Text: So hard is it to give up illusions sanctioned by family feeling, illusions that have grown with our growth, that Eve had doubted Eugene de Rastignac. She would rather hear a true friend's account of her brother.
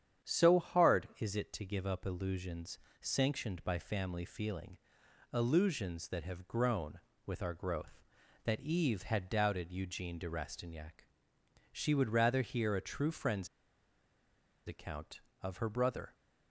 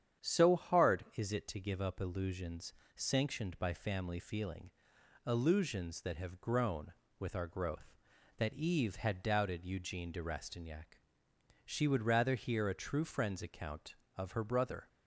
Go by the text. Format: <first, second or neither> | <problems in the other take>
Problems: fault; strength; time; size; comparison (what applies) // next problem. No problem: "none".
second | starts louder than the rest; strong; until 1.3 s; 8.5 dB; strong in the second // pauses between "illusions" and "sanctioned"; slight; at 2.7 s; 0.22 s long; slight in the second // pauses between "friend's" and "account"; at 13.4 s; 1.1 s long